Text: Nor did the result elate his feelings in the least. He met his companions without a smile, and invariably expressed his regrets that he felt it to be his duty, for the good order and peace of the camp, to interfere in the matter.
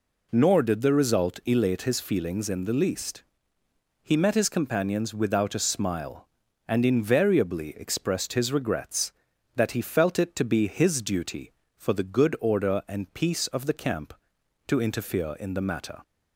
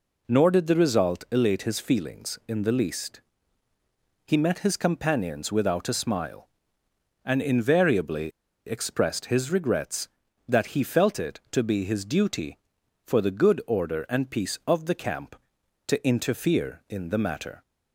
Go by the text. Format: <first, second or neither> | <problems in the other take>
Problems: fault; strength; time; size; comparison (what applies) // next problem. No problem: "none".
first | pauses between "invariably" and "expressed"; at 8.3 s; 0.36 s long